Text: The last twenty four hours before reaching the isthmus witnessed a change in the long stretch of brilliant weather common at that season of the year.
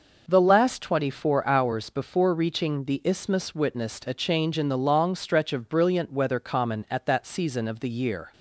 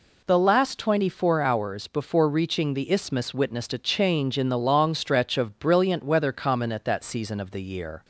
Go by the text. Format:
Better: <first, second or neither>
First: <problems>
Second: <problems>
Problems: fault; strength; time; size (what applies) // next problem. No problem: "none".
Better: neither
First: none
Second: none